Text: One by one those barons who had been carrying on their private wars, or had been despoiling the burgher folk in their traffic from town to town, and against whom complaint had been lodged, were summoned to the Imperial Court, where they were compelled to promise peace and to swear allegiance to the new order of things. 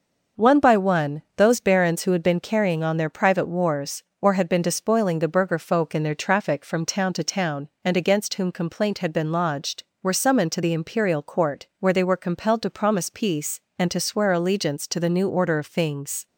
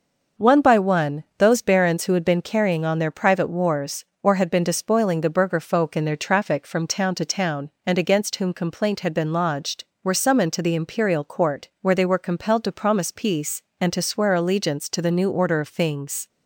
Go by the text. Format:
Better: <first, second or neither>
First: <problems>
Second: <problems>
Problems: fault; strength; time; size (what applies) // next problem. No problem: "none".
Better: neither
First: starts louder than the rest; noticeable; until 1.5 s; 6 dB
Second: starts louder than the rest; noticeable; until 1.5 s; 6 dB